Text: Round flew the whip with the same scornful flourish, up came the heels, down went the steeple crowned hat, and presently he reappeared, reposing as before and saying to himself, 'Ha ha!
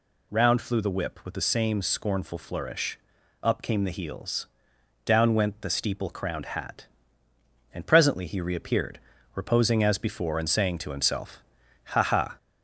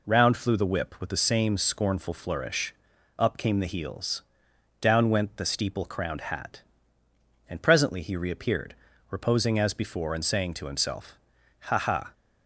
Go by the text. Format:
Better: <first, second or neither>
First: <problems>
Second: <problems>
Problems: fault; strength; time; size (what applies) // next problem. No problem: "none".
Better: second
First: gets louder; slight; throughout; 2 dB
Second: none